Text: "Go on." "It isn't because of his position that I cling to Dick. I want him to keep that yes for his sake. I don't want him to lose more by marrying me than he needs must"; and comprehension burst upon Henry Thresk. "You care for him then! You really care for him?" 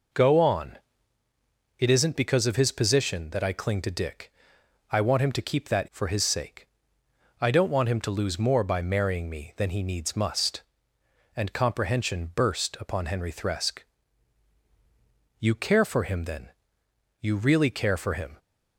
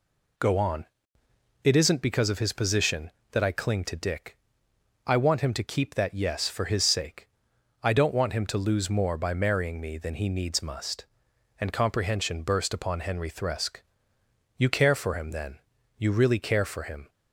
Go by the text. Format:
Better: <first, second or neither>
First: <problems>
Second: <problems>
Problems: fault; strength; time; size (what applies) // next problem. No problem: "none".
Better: second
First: skips "yes"; at 5.8 s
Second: none